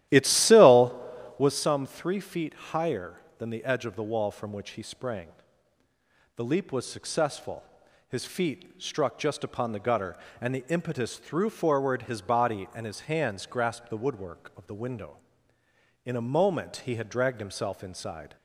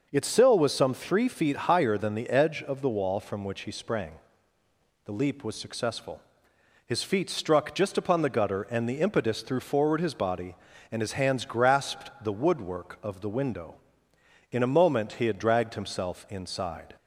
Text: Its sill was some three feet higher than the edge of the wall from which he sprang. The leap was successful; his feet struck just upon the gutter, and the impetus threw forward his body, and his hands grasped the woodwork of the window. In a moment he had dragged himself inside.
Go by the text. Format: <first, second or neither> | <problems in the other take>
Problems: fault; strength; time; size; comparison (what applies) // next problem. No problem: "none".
second | starts louder than the rest; strong; until 1.6 s; 13.5 dB